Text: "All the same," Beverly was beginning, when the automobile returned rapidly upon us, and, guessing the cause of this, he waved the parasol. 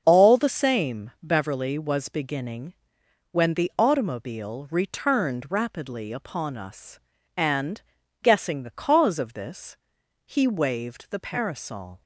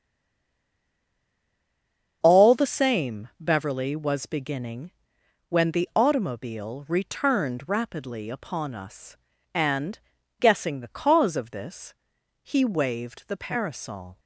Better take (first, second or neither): first